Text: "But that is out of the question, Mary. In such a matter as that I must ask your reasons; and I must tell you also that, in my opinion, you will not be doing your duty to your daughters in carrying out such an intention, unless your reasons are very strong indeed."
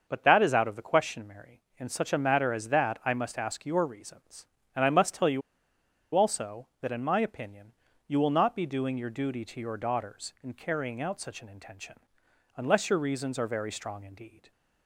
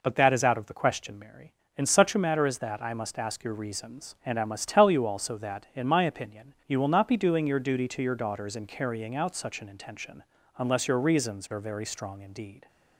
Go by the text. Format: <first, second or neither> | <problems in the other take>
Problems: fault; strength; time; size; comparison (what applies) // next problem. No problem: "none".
second | starts louder than the rest; until 1.0 s; 6.5 dB // pauses between "you" and "also"; noticeable; at 5.4 s; 0.73 s long